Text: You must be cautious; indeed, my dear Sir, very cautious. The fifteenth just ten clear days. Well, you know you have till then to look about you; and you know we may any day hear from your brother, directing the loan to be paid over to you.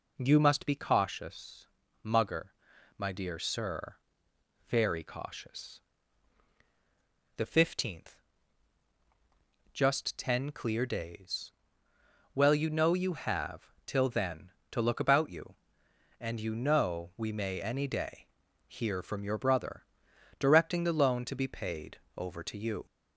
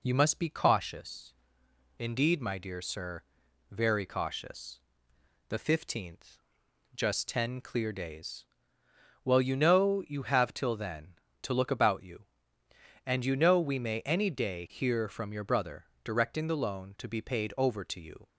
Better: second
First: says "mugger" for "indeed"; at 2.0 s // pauses between "fifteenth" and "just"; strong; at 8.1 s; 1.5 s long // pauses between "day" and "hear"; at 18.2 s; 0.40 s long // pauses between "paid" and "over"; slight; at 21.9 s; 0.18 s long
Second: pauses between "fifteenth" and "just"; noticeable; at 6.3 s; 0.54 s long

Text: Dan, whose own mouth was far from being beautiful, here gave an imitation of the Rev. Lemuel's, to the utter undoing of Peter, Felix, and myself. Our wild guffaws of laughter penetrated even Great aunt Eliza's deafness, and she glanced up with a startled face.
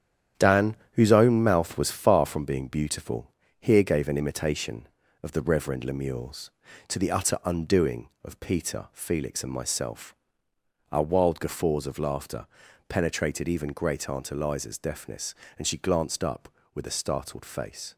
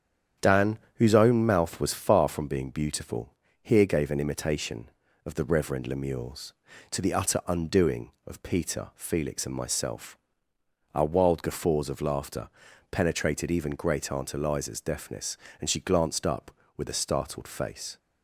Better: second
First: gets quieter; throughout; 6.5 dB // starts louder than the rest; strong; until 1.5 s; 9.5 dB // pauses between "laughter" and "penetrated"; at 12.4 s; 0.42 s long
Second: starts louder than the rest; strong; until 1.5 s; 8.5 dB // pauses between "laughter" and "penetrated"; at 12.4 s; 0.42 s long

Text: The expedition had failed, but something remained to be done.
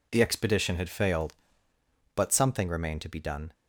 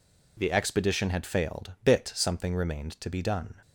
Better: first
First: none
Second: says "bit" for "but"; at 1.8 s

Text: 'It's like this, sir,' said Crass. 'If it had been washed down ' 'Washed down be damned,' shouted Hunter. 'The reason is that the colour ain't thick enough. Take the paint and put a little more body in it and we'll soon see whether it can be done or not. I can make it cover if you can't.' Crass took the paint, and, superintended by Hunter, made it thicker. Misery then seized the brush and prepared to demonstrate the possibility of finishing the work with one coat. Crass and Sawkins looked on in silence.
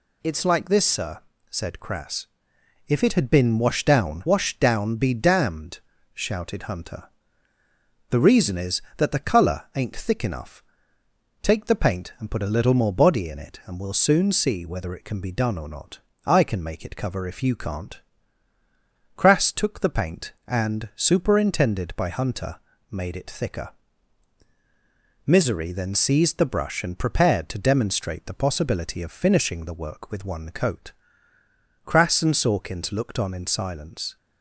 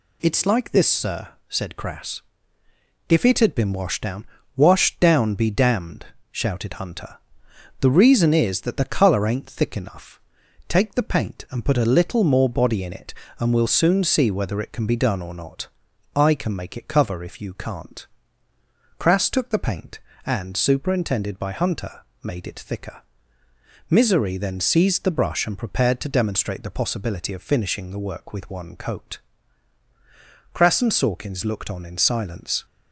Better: neither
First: none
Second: none

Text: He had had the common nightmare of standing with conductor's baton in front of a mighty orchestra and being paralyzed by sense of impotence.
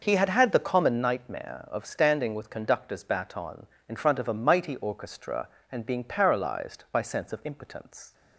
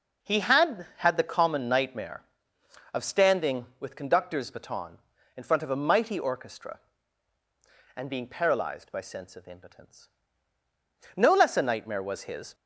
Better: first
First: none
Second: goes on to say "No less a nightmare was his"; from 11.1 s on; 1.3 s long

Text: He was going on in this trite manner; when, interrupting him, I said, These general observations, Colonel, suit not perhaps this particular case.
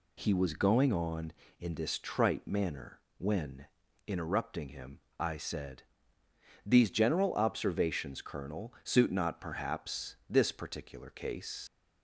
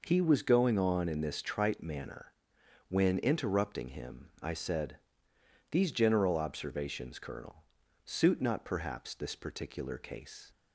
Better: second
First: leaves "case" unfinished; at 11.6 s; 90 ms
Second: none

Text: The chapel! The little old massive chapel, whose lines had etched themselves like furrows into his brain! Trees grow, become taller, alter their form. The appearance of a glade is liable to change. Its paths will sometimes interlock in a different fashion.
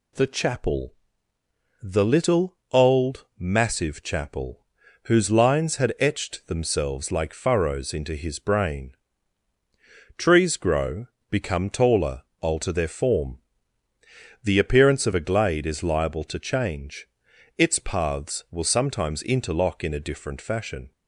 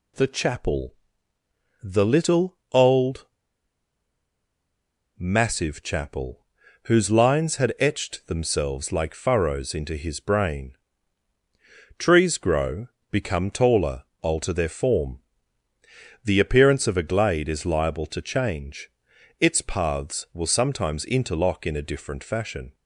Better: first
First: none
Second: pauses between "old" and "massive"; strong; at 3.2 s; 1.9 s long

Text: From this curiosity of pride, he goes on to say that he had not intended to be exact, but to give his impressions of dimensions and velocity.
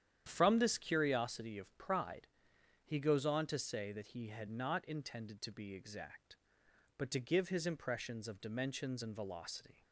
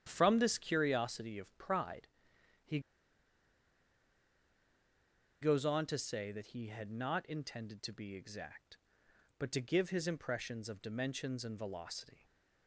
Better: first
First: starts louder than the rest; strong; until 1.2 s; 9.5 dB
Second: starts louder than the rest; strong; until 1.0 s; 9.5 dB // pauses between "he" and "goes"; strong; at 2.7 s; 2.6 s long // stays silent after the last word; slight; from 12.1 s on; 0.5 s long

